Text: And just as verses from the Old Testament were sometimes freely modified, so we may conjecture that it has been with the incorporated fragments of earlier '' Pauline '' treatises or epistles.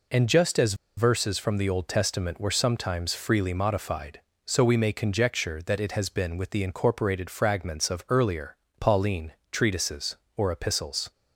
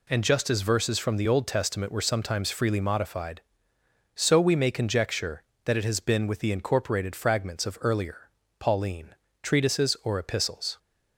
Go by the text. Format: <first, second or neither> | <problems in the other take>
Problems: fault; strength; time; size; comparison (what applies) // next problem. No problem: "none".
second | pauses between "as" and "verses"; slight; at 0.7 s; 0.23 s long